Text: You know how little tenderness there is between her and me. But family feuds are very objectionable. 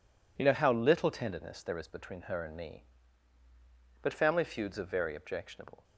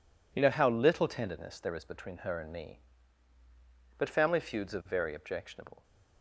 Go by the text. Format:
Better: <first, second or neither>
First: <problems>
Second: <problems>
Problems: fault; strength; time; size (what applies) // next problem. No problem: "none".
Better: neither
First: none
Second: none